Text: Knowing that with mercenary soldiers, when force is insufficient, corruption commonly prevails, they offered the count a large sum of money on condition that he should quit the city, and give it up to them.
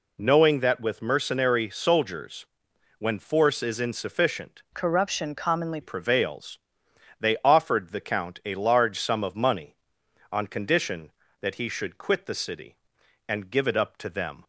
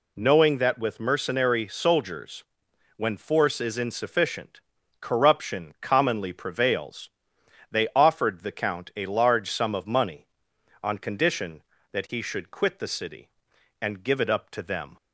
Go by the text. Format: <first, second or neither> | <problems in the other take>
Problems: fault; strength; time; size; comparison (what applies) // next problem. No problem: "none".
second | changes voice from "corruption" to "commonly"; from 4.7 to 5.8 s; 1.1 s long